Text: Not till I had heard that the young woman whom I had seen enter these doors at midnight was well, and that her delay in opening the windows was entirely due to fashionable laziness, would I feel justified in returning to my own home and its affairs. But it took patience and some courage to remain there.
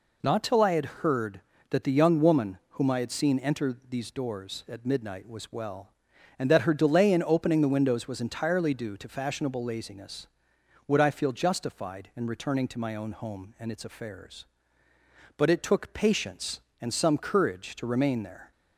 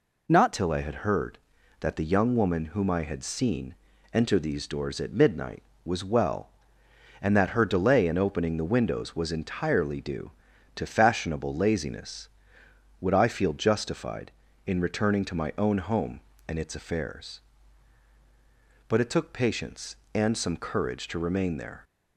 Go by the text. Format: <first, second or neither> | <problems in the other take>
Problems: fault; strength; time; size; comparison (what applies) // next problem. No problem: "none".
first | changes voice at "till"; from 0.5 s on; 21.3 s long // pauses between "seen" and "enter"; at 3.7 s; 0.40 s long